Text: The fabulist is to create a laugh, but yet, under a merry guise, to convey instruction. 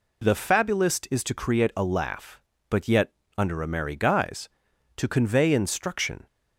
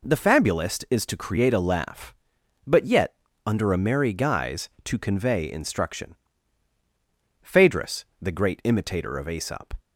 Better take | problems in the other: first | goes on to say "Phaedrus the great imitator of Aesop"; strong; from 7.4 s on; 2.3 s long

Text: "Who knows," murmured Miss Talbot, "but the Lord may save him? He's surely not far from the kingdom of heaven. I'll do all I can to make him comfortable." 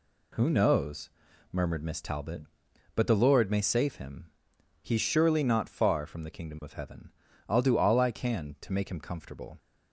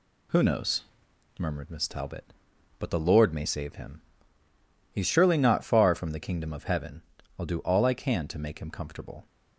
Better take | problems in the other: neither | none

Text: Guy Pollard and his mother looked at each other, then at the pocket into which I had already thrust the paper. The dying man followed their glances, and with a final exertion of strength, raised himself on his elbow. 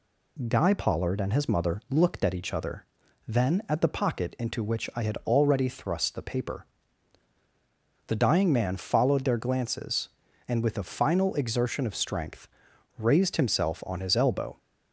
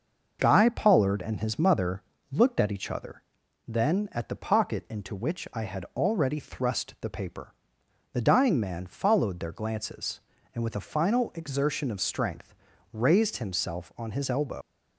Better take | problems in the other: first | starts louder than the rest; noticeable; until 1.4 s; 6 dB // pauses between "mother" and "looked"; slight; at 2.0 s; 0.30 s long // leaves "elbow" unfinished; at 14.6 s; 90 ms

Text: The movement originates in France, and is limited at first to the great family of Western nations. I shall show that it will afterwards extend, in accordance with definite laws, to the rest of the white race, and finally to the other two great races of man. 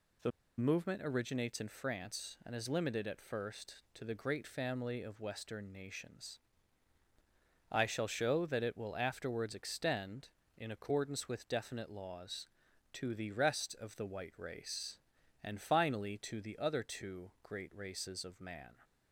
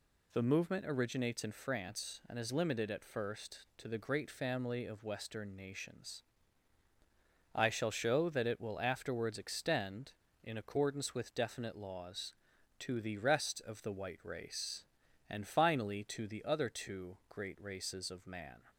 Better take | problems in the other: second | pauses between "The" and "movement"; slight; at 0.3 s; 0.28 s long

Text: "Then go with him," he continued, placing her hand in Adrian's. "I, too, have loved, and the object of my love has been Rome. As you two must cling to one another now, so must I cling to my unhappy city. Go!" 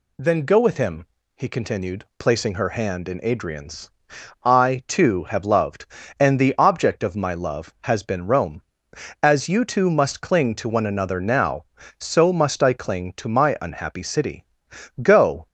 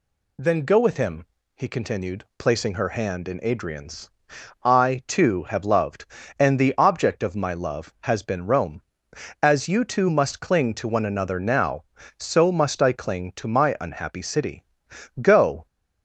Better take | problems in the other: neither | none

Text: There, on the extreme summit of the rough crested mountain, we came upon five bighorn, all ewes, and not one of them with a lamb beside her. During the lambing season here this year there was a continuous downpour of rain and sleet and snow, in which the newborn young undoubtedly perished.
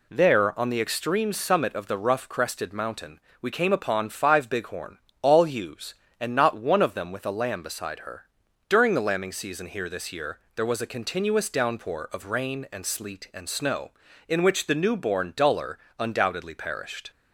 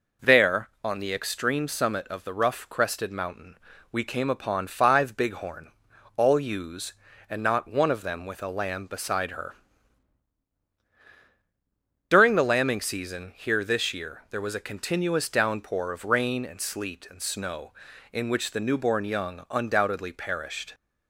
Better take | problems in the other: second | pauses between "year" and "there"; slight; at 10.3 s; 0.16 s long // says "duller" for "young"; at 15.3 s

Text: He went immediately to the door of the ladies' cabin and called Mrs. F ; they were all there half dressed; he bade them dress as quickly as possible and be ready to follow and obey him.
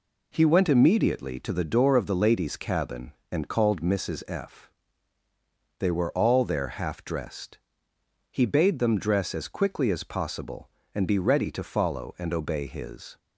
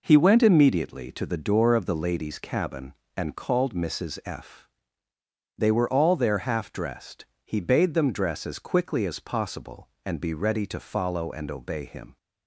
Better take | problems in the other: second | says "his" for "him"; at 12.6 s

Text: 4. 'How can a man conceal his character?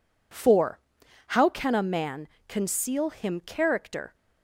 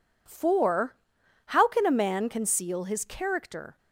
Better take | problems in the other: second | pauses between "man" and "conceal"; slight; at 2.2 s; 0.18 s long // says "him" for "his"; at 3.1 s

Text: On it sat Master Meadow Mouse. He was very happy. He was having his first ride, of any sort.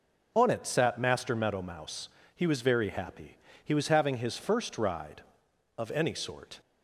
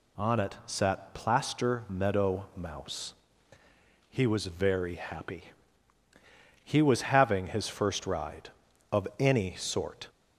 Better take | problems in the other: first | says "Plaster" for "Master"; at 1.1 s

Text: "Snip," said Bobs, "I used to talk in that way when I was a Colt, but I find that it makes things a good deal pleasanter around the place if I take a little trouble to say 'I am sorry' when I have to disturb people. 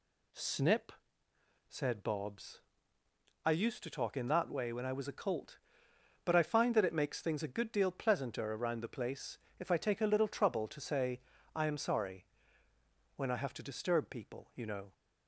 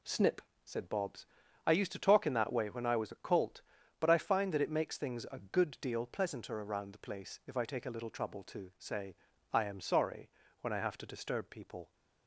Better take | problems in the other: second | pauses between "place" and "if"; slight; at 9.3 s; 0.20 s long // pauses between "say" and "I"; slight; at 11.1 s; 0.34 s long; also in the second // pauses between "sorry" and "when"; noticeable; at 12.2 s; 0.90 s long; slight in the second // goes on to say "You know"; slight; from 14.5 s on; 0.38 s long

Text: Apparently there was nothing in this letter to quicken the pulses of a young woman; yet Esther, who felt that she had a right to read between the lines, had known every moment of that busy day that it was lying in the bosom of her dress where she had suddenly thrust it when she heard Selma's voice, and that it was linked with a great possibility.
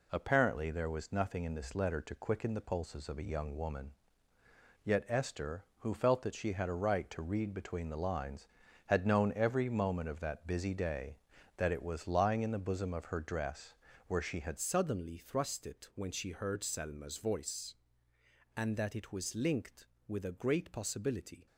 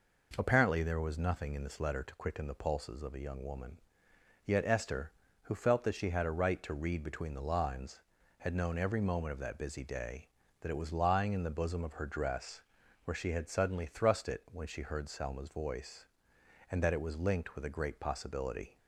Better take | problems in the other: second | pauses between "dress" and "where"; slight; at 13.7 s; 0.32 s long; also in the second // changes voice at "suddenly"; from 14.5 s on; 6.9 s long

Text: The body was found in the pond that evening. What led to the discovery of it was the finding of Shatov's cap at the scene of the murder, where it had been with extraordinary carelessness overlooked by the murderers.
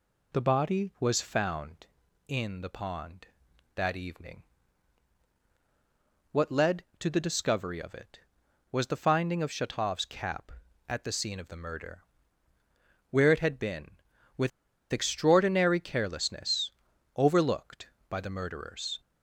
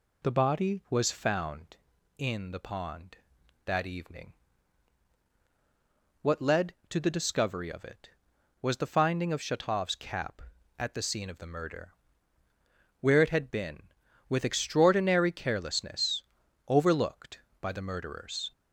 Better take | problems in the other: second | pauses between "with" and "extraordinary"; at 14.5 s; 0.41 s long // pauses between "carelessness" and "overlooked"; noticeable; at 16.7 s; 0.46 s long; noticeable in the second

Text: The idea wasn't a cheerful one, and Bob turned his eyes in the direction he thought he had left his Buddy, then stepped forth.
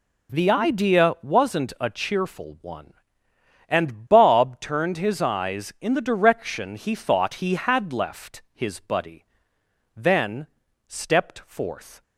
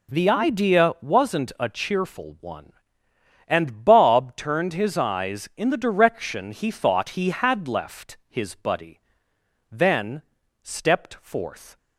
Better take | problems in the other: neither | pauses between "then" and "stepped"; the same in both

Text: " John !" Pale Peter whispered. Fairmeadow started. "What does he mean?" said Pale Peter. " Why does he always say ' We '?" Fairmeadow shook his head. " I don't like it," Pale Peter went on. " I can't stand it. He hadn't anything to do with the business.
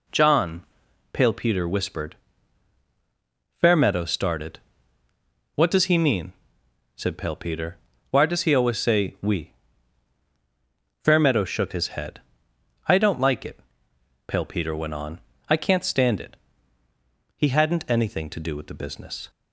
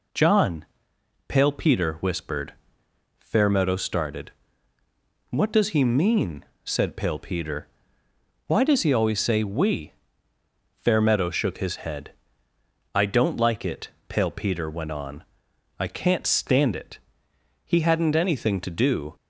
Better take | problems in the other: first | stops before "with the business"; at 19.1 s

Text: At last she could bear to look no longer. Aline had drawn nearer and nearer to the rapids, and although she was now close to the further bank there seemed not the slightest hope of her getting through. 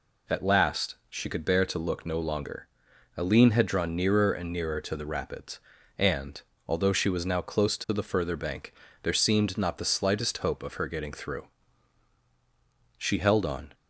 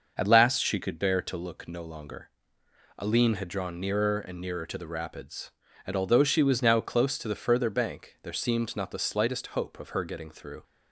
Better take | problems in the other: second | pauses between "and" and "although"; slight; at 6.4 s; 0.26 s long // pauses between "bank" and "there"; slight; at 8.7 s; 0.30 s long // goes on to say "She held on"; noticeable; from 12.9 s on; 0.78 s long

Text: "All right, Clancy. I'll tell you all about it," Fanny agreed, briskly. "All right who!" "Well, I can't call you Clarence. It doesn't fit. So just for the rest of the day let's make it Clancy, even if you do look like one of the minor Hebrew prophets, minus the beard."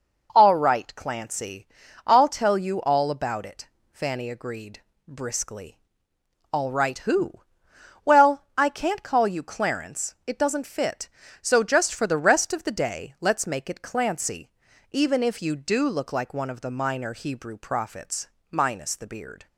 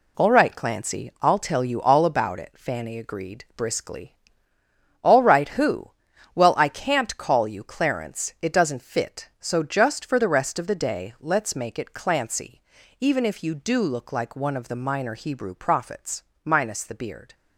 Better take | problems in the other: first | gets quieter; strong; throughout; 7.5 dB

